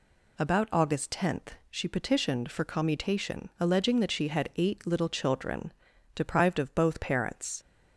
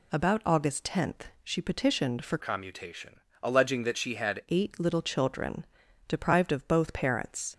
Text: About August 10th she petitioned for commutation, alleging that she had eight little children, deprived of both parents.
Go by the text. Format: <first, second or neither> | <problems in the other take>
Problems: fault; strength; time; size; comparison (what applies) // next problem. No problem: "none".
first | changes voice from "commutation" to "had"; from 2.4 to 4.4 s; 2.0 s long